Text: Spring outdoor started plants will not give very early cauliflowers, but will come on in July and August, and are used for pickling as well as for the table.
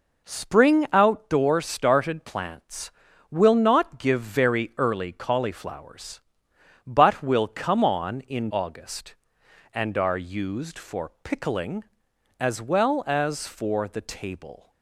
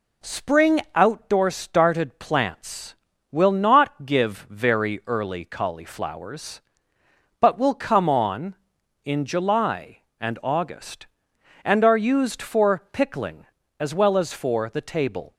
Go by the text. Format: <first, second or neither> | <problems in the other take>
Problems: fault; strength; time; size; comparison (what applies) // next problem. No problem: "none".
second | skips "July and"; at 8.4 s